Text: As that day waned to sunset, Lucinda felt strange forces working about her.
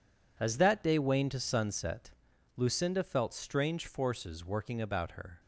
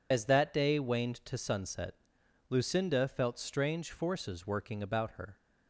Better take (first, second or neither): first